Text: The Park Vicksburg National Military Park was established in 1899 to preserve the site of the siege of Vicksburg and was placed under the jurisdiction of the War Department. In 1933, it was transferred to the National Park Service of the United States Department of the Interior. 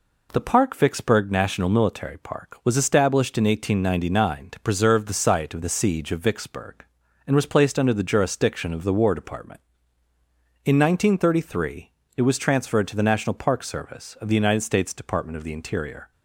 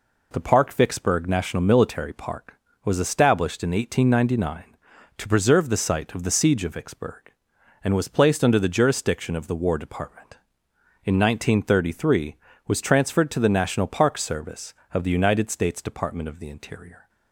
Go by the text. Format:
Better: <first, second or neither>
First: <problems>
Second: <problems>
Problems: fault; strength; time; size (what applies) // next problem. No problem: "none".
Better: first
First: none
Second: skips "it"; at 12.5 s